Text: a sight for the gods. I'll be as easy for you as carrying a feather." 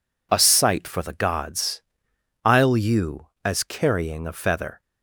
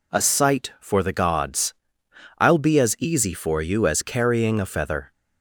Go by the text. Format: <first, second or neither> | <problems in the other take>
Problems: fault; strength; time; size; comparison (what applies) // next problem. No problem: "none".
second | skips "be as easy for"; at 2.7 s